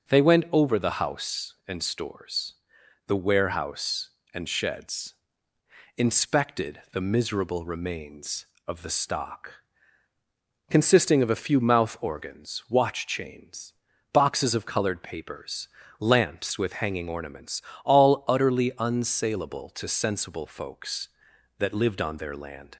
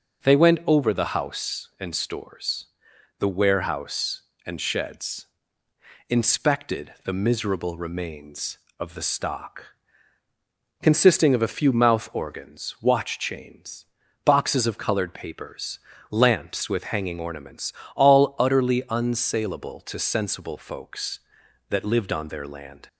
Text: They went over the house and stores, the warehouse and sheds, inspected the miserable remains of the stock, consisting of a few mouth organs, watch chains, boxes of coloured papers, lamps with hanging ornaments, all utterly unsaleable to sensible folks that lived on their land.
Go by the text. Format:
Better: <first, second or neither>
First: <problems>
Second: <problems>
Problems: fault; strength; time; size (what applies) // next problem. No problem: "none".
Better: neither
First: none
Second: none